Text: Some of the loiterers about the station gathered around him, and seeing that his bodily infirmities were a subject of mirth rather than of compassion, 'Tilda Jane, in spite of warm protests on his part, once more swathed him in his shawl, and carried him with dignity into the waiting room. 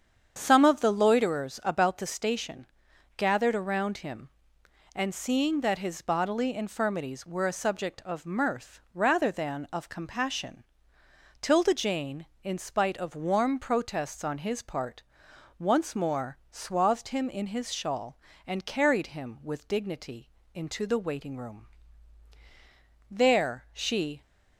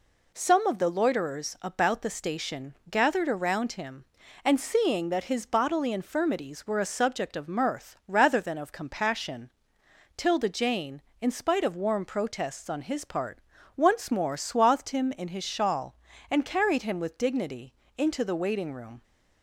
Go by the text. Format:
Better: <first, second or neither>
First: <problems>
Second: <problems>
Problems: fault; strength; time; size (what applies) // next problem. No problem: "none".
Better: second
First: starts louder than the rest; strong; until 1.3 s; 8 dB // pauses between "station" and "gathered"; noticeable; at 2.6 s; 0.50 s long // pauses between "dignity" and "into"; slight; at 20.2 s; 0.24 s long // goes on to say "There she"; noticeable; from 23.0 s on; 1.1 s long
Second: pauses between "dignity" and "into"; slight; at 17.7 s; 0.24 s long